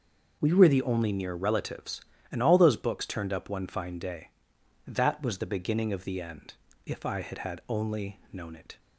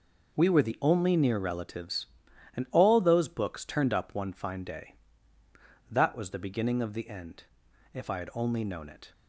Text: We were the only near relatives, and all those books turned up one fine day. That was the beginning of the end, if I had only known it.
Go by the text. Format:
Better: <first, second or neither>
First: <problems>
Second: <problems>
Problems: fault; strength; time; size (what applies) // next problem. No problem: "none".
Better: second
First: says "had" twice; at 7.3 s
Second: none